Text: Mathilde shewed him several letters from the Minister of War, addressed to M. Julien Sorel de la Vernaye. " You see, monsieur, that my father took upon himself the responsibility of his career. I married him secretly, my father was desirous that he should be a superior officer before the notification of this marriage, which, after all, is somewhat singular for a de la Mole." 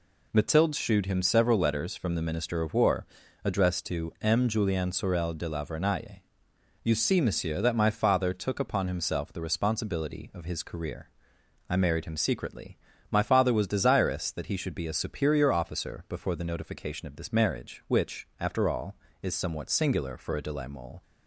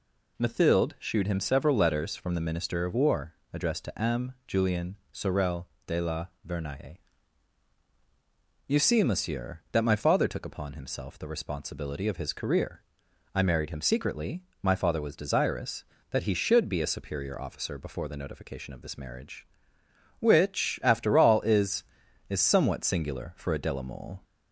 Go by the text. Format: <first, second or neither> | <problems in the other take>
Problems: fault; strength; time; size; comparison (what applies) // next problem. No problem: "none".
first | pauses between "Julien" and "Sorel"; slight; at 4.9 s; 0.16 s long // pauses between "Sorel" and "de"; slight; at 5.6 s; 0.20 s long // pauses between "la" and "Vernaye"; slight; at 6.2 s; 0.20 s long // says "is" twice; at 22.2 s